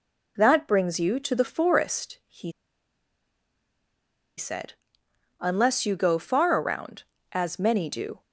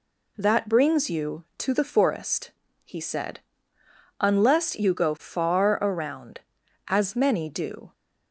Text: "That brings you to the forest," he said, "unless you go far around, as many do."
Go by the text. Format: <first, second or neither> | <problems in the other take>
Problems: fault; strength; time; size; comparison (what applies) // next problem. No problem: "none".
second | pauses between "he" and "said"; strong; at 2.5 s; 1.8 s long